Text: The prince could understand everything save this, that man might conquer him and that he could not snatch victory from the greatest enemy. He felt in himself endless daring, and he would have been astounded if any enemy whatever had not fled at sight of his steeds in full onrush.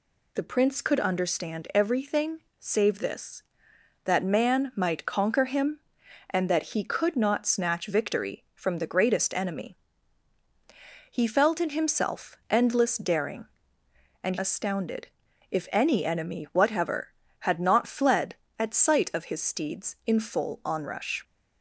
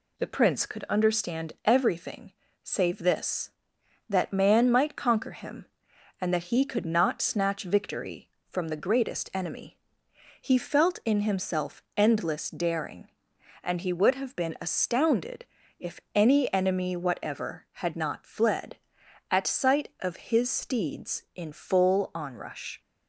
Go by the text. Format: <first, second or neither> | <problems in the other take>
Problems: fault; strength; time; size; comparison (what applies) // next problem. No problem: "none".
second | pauses between "everything" and "save"; slight; at 2.3 s; 0.20 s long; slight in the second // skips "he would have been"; at 14.3 s // pauses between "astounded" and "if"; at 15.0 s; 0.42 s long; slight in the second